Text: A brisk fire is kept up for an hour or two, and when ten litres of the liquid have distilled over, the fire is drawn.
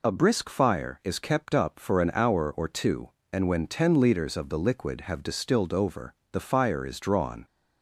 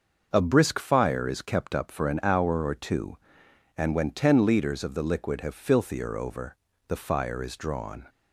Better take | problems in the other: first | starts louder than the rest; until 1.3 s; 6.5 dB // says "filthier" for "distilled"; at 5.5 s

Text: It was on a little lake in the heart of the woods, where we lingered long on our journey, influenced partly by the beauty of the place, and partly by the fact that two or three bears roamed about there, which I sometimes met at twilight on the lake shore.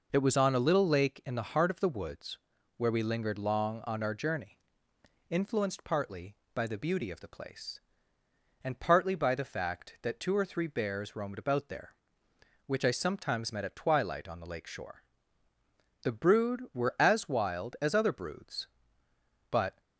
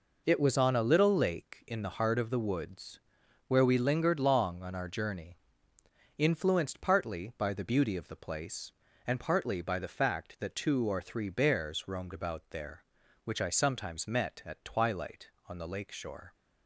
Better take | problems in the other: second | goes on to say "The brood were as wild as other broods but"; strong; from 16.0 s on; 3.7 s long

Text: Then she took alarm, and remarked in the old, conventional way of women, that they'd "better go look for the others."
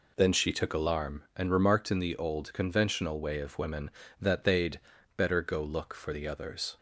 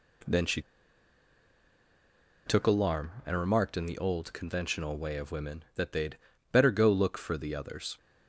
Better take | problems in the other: first | pauses between "she" and "took"; strong; at 0.6 s; 1.8 s long // pauses between "they'd" and "better"; slight; at 6.1 s; 0.32 s long; also in the first

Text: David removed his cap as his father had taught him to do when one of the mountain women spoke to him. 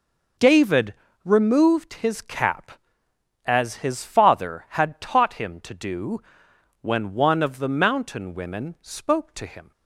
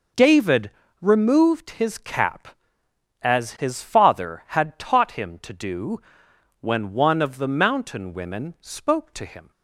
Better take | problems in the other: neither | pauses between "David" and "removed"; slight; the same in both // pauses between "do" and "when"; noticeable; the same in both

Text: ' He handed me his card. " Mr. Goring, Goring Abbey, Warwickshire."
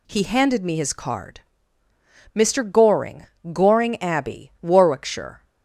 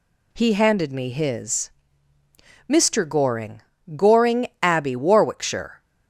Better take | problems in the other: first | skips "card"; at 1.9 s // pauses between "Goring" and "Abbey"; slight; at 4.4 s; 0.16 s long

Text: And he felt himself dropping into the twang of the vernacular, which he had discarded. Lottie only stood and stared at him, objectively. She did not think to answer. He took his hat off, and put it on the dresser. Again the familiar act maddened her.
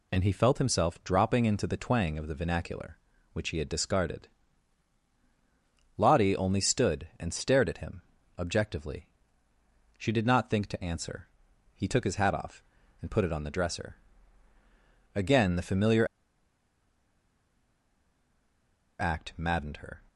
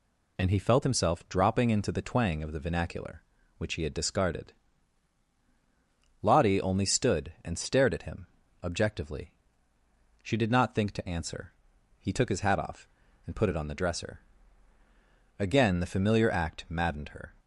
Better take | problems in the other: second | pauses between "familiar" and "act"; strong; at 16.0 s; 2.9 s long

